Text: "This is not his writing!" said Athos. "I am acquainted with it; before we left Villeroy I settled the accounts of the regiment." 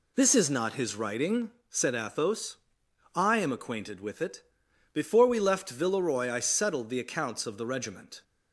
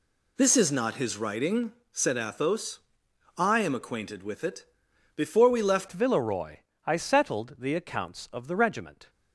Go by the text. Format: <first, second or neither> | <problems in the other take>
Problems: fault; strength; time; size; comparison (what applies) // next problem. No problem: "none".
first | changes voice at "Villeroy"; from 5.8 s on; 3.2 s long // pauses between "Villeroy" and "I"; slight; at 6.5 s; 0.28 s long